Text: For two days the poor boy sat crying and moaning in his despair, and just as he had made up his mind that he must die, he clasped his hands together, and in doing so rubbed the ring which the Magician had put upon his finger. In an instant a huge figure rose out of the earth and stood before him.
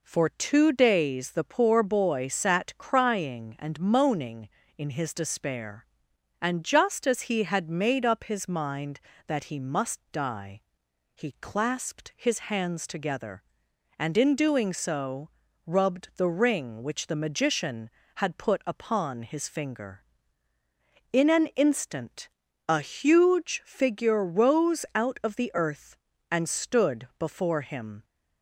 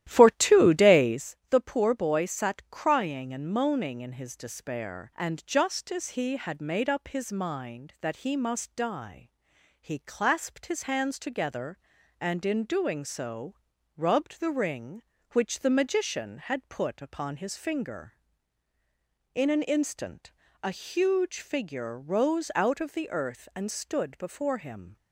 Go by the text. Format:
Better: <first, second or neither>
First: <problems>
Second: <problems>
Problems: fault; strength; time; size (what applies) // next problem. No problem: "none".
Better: first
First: pauses between "so" and "rubbed"; slight; at 15.3 s; 0.36 s long // pauses between "instant" and "a"; at 22.2 s; 0.40 s long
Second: starts louder than the rest; strong; until 1.3 s; 13 dB // pauses between "so" and "rubbed"; at 13.5 s; 0.42 s long // pauses between "instant" and "a"; slight; at 20.3 s; 0.32 s long